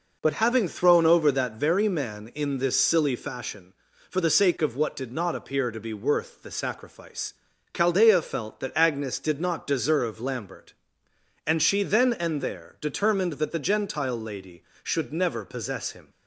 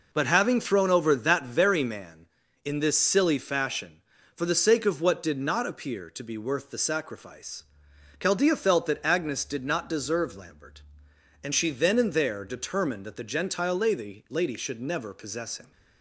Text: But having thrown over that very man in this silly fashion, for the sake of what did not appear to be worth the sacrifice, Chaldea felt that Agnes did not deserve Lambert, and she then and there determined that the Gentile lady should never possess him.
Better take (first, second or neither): first